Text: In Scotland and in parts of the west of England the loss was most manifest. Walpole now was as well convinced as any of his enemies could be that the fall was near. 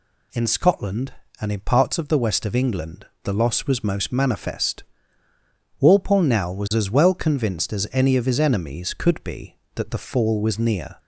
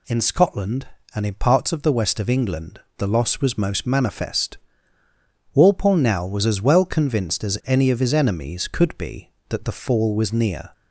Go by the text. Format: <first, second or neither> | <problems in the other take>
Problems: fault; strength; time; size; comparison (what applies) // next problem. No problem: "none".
neither | pauses between "England" and "the"; slight; the same in both